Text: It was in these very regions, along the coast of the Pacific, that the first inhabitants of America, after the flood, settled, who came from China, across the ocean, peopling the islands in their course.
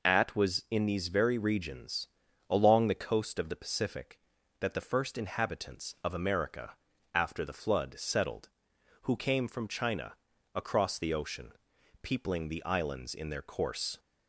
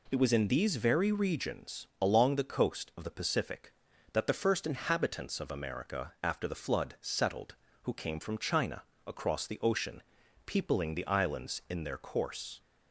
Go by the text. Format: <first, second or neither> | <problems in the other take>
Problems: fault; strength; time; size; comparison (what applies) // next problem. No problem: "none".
second | says "At" for "It"; at 0.0 s